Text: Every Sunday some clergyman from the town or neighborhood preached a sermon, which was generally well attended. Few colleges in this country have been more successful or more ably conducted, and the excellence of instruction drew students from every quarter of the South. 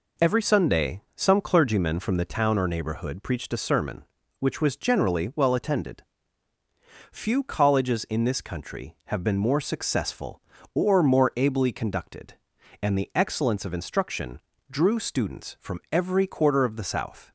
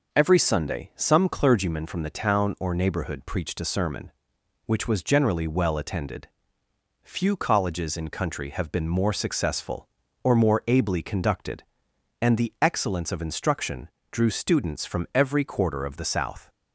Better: first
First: pauses between "instruction" and "drew"; slight; at 14.3 s; 0.32 s long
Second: skips "this"; at 8.0 s // pauses between "instruction" and "drew"; slight; at 13.8 s; 0.24 s long

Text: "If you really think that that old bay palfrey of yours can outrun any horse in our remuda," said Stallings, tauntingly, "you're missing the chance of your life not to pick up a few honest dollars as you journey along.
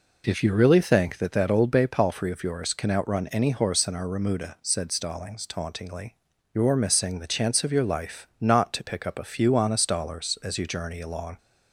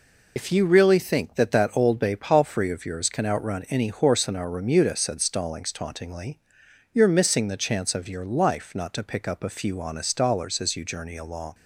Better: first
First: none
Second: loses the start of "If"; at 0.3 s; 55 ms

